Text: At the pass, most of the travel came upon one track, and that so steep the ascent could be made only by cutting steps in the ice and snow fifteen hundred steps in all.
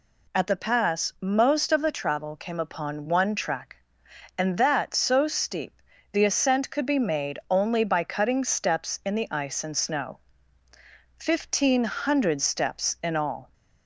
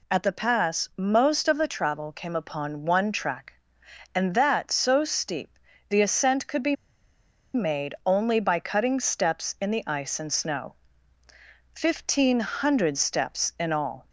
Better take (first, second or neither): first